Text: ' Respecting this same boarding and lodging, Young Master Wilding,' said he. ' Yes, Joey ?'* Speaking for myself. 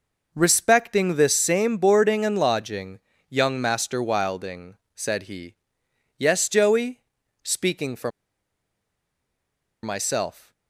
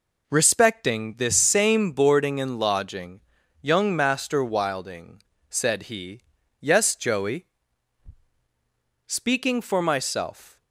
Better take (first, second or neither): second